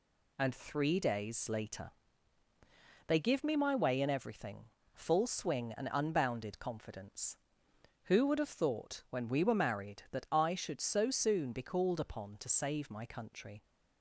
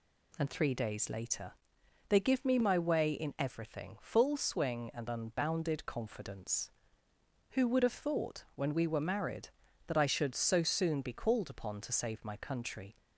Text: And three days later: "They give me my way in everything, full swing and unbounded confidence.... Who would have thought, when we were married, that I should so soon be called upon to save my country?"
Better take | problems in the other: neither | none

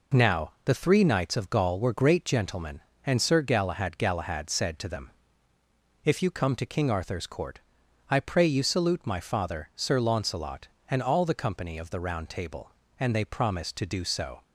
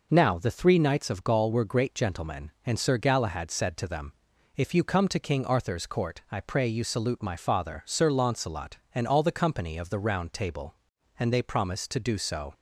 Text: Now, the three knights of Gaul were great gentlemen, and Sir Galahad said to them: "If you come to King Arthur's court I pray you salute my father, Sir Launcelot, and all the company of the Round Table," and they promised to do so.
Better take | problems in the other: second | says "Galahad" twice; at 3.9 s // pauses between "court" and "I"; noticeable; at 7.6 s; 0.50 s long

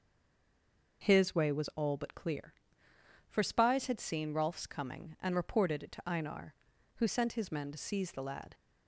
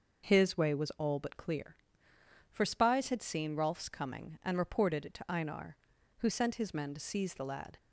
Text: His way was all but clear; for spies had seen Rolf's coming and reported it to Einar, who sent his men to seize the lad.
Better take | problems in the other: second | stays silent before the first word; until 1.0 s; 1.0 s long

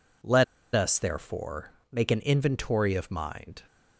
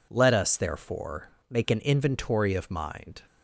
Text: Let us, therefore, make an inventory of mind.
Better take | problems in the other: second | pauses between "Let" and "us"; slight; at 0.4 s; 0.31 s long

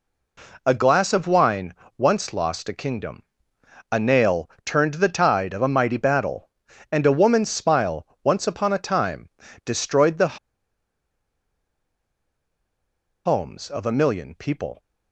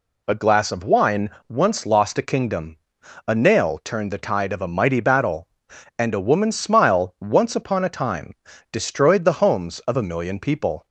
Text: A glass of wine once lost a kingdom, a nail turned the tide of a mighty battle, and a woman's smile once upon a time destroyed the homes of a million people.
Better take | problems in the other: second | pauses between "wine" and "once"; slight; at 1.7 s; 0.22 s long; slight in the second // pauses between "nail" and "turned"; slight; at 4.4 s; 0.16 s long // pauses between "smile" and "once"; slight; at 8.0 s; 0.16 s long // pauses between "time" and "destroyed"; slight; at 9.3 s; 0.34 s long; slight in the second // pauses between "the" and "homes"; strong; at 10.3 s; 2.8 s long

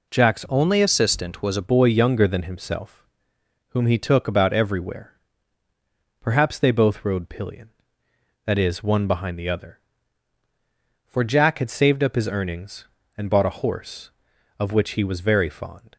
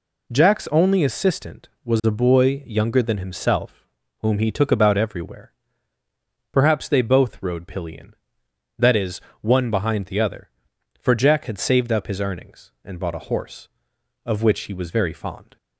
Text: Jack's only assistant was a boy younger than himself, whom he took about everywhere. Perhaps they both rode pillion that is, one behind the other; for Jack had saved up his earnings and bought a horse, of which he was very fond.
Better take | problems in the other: second | changes voice from "only" to "a"; from 0.4 to 1.6 s; 1.2 s long

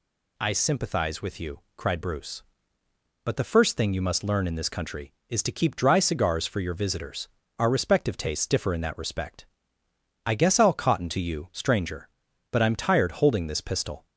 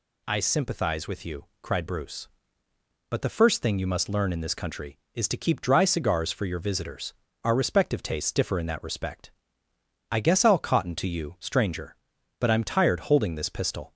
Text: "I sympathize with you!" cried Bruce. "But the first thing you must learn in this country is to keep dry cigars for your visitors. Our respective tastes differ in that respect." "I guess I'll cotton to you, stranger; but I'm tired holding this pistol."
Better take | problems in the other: neither | none

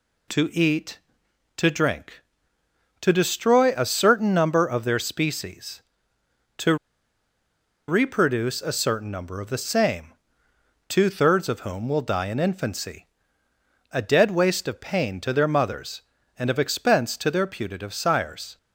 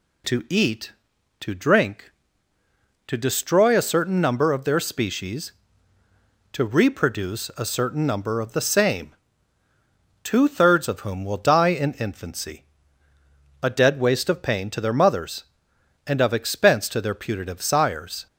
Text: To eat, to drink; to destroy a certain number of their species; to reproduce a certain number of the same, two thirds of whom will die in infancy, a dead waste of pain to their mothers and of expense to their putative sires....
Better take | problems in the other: second | pauses between "to" and "reproduce"; at 6.7 s; 1.1 s long

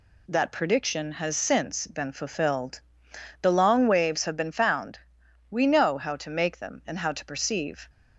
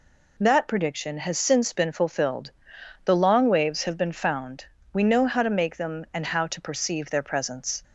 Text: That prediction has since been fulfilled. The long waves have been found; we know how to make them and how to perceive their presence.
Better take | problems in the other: second | stops before "their presence"; at 7.8 s

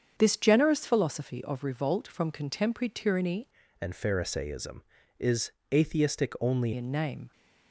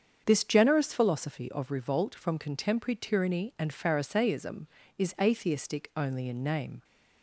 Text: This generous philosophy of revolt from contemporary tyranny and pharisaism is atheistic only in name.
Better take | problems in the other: second | starts louder than the rest; strong; until 1.1 s; 7.5 dB; strong in the second // changes voice from "and" to "only"; from 3.8 to 6.7 s; 2.9 s long // pauses between "is" and "atheistic"; slight; at 5.5 s; 0.20 s long

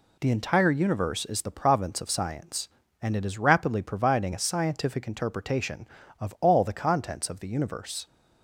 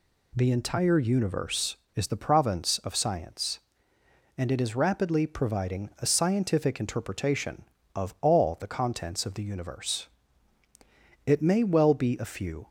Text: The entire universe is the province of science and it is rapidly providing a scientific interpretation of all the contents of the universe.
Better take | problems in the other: first | goes on to say "It may well be a few"; from 11.2 s on; 1.4 s long

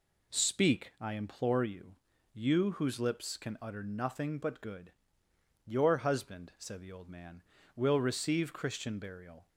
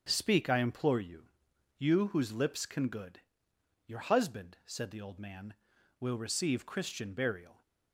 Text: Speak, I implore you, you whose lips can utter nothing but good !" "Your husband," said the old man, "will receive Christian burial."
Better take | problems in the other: first | skips "utter nothing but"; at 2.8 s

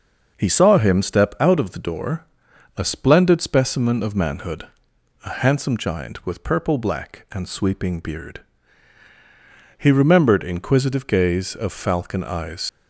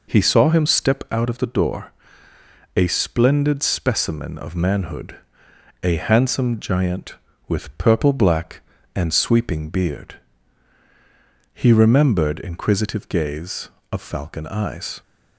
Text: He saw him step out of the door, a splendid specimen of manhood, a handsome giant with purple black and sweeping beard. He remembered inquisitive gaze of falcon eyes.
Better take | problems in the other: second | starts louder than the rest; noticeable; until 1.3 s; 6 dB // leaves "eyes" unfinished; at 12.6 s; 100 ms

